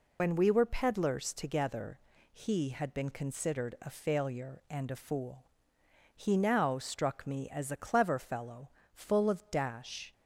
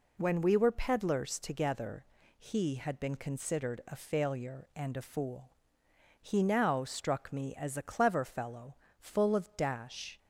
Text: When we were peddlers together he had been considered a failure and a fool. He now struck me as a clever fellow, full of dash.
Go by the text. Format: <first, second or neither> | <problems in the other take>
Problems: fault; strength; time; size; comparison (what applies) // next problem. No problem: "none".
second | loses the start of "When"; at 0.1 s; 80 ms // pauses between "together" and "he"; slight; at 1.9 s; 0.32 s long; slight in the second